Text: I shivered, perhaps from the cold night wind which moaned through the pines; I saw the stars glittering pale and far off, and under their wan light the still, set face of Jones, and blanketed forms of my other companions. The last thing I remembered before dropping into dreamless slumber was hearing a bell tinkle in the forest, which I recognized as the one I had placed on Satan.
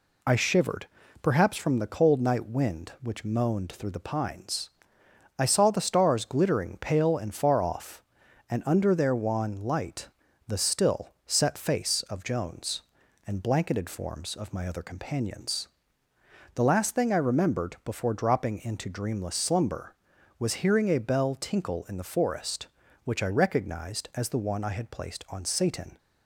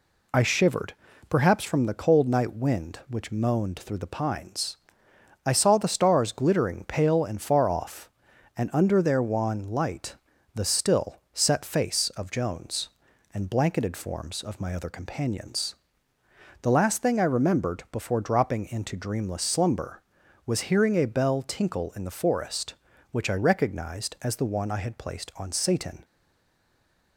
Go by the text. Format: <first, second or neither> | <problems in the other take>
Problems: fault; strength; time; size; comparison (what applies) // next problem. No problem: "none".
first | pauses between "light" and "the"; slight; at 10.1 s; 0.36 s long; slight in the first // stays silent after the last word; from 26.0 s on; 1.1 s long